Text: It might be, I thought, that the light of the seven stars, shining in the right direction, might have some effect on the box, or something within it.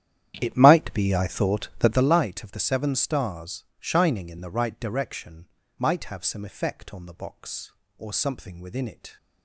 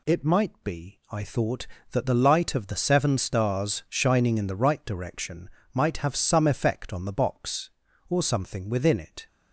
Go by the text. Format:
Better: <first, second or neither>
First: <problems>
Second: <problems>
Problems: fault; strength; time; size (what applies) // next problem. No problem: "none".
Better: second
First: starts louder than the rest; strong; until 2.1 s; 10.5 dB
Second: none